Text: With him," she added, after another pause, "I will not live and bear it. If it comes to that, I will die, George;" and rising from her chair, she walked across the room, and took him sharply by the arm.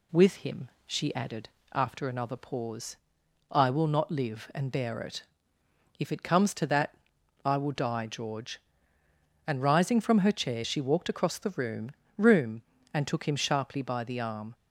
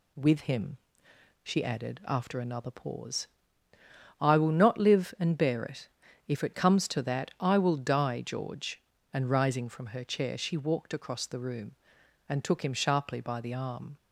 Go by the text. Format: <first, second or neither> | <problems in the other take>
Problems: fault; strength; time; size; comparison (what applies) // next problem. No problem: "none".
second | says "room" twice; at 12.1 s